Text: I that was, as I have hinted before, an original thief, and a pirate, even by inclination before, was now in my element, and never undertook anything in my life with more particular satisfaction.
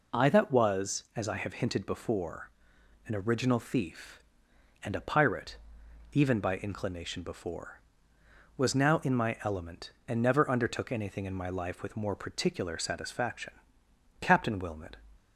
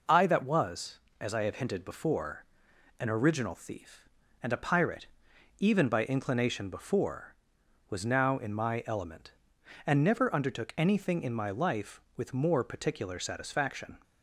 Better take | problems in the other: second | goes on to say "Captain Wilmot"; noticeable; from 14.2 s on; 0.74 s long

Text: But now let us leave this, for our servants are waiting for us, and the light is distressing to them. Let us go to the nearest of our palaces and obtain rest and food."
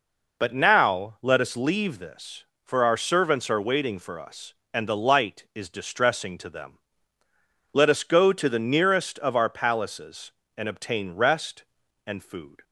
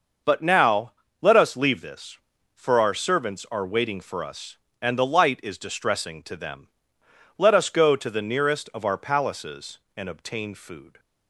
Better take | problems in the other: first | starts louder than the rest; noticeable; until 1.5 s; 6 dB // pauses between "now" and "let"; slight; at 0.9 s; 0.28 s long // skips "rest and"; at 10.5 s

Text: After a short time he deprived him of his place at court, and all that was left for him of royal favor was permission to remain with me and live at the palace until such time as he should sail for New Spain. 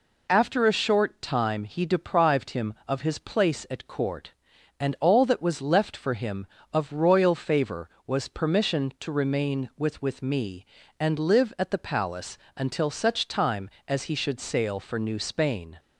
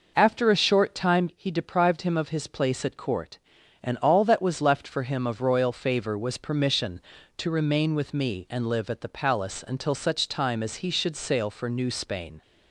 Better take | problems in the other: second | says "with" twice; at 10.0 s // pauses between "palace" and "until"; slight; at 12.3 s; 0.18 s long

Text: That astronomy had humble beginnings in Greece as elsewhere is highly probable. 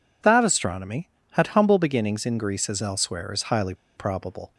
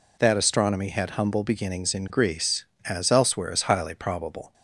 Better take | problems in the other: second | pauses between "highly" and "probable"; slight; at 3.7 s; 0.23 s long

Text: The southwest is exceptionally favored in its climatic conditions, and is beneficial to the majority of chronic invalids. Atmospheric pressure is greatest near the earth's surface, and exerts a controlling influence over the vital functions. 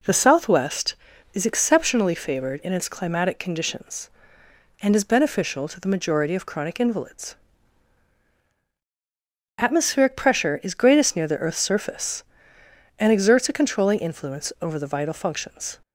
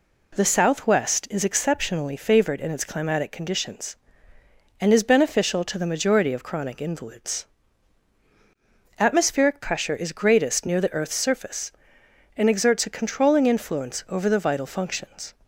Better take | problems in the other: neither | none

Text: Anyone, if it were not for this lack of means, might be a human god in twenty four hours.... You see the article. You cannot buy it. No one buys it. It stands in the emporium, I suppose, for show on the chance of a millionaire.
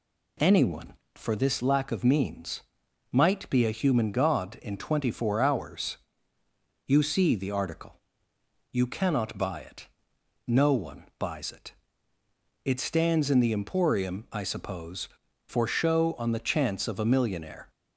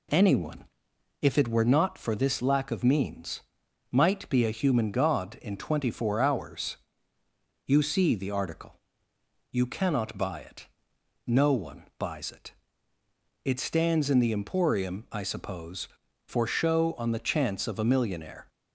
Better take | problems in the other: second | skips "if it were not"; at 1.0 s // pauses between "one" and "buys"; slight; at 11.0 s; 0.16 s long; slight in the second

